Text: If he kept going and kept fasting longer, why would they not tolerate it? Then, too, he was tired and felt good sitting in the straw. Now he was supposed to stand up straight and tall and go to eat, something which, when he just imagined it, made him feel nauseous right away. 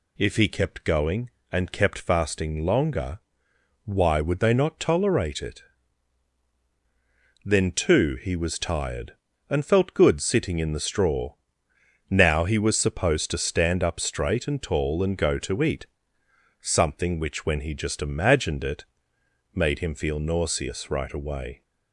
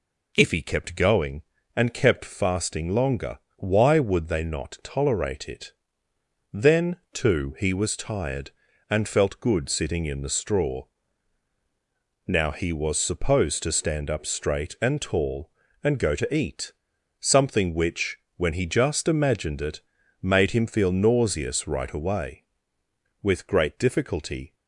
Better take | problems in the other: first | goes on to say "With great difficulty"; from 23.2 s on; 1.3 s long

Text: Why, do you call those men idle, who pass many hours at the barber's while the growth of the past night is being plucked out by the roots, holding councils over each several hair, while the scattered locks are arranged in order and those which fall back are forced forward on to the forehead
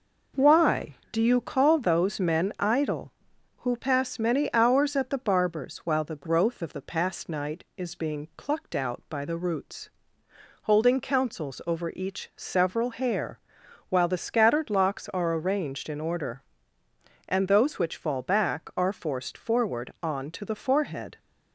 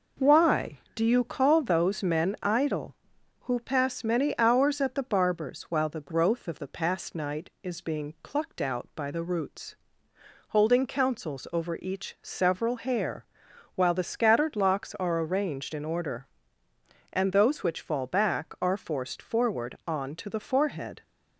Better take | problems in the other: neither | none

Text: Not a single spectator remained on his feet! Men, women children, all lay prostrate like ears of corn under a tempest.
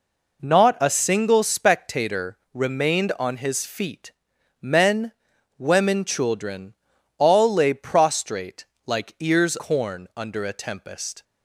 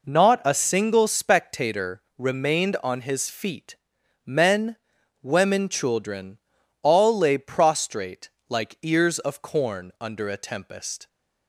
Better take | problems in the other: second | pauses between "spectator" and "remained"; slight; at 2.3 s; 0.16 s long; slight in the second // pauses between "prostrate" and "like"; slight; at 8.6 s; 0.22 s long; slight in the second // skips "of"; at 9.5 s

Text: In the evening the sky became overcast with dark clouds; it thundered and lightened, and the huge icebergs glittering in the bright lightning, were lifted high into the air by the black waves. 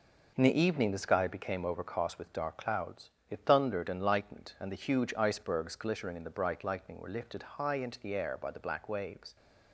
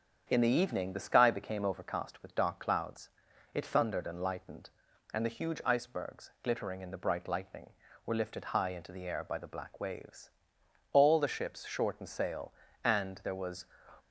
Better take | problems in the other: first | starts louder than the rest; strong; until 1.3 s; 7.5 dB // goes on to say "All the ships shortened sail and there was"; strong; from 10.9 s on; 2.7 s long

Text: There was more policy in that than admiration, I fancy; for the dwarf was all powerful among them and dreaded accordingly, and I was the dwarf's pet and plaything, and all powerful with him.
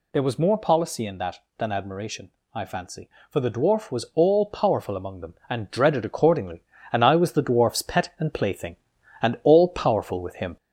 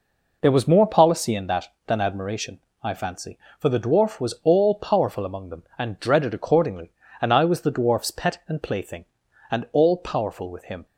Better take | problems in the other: second | gets louder; slight; throughout; 2.5 dB

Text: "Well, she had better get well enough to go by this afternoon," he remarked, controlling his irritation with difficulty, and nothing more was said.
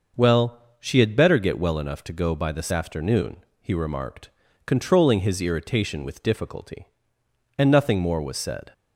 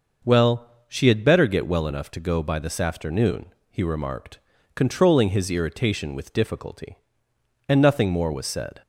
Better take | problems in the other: neither | none

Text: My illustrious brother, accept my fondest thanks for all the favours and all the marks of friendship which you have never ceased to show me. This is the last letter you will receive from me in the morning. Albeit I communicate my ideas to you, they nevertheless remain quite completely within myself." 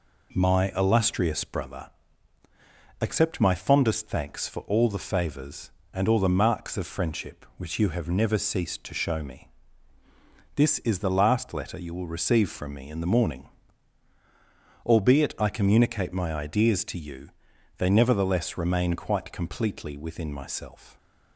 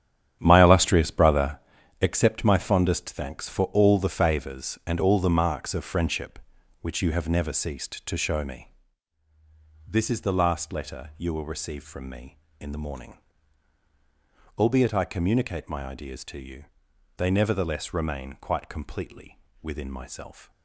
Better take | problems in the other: first | starts louder than the rest; strong; until 2.2 s; 10 dB // pauses between "completely" and "within"; slight; at 19.3 s; 0.24 s long

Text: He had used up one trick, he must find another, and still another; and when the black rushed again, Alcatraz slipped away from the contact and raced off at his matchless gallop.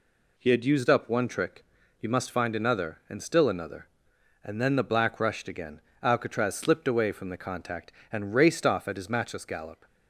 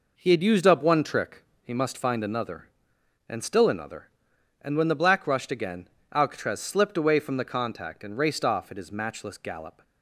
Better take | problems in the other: second | says "then" for "when"; at 4.6 s

